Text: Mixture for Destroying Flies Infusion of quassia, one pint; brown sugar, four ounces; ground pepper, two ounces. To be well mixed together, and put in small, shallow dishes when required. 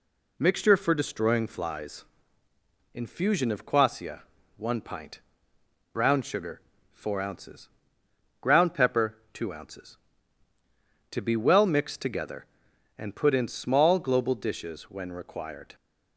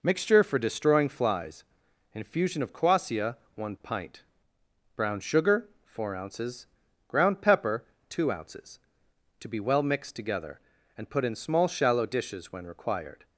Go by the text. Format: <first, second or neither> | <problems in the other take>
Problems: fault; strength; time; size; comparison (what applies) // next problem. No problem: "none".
second | pauses between "Flies" and "Infusion"; noticeable; at 2.0 s; 0.90 s long; noticeable in the second // says "global" for "shallow"; at 13.9 s